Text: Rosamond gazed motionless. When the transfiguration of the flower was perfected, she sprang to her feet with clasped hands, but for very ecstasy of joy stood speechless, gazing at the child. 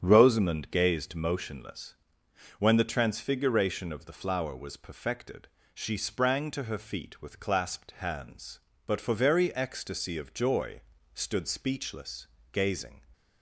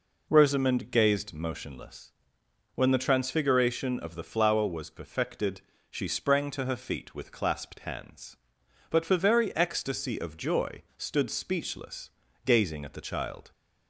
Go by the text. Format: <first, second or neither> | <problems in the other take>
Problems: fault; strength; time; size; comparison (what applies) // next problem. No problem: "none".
second | starts louder than the rest; strong; until 1.0 s; 8 dB // pauses between "joy" and "stood"; slight; at 10.8 s; 0.32 s long; slight in the second // stops before "at the child"; at 13.1 s